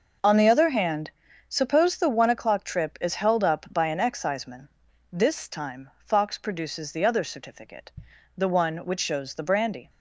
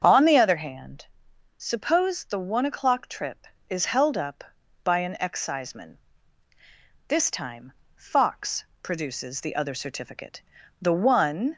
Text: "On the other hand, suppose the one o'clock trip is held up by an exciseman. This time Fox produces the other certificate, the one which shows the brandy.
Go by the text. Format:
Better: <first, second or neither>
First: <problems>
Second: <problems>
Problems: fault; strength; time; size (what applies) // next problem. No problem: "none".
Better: first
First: none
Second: starts louder than the rest; until 1.0 s; 7 dB // pauses between "time" and "Fox"; slight; at 7.7 s; 0.24 s long // pauses between "Fox" and "produces"; slight; at 8.6 s; 0.18 s long // stops before "which shows the brandy"; at 11.5 s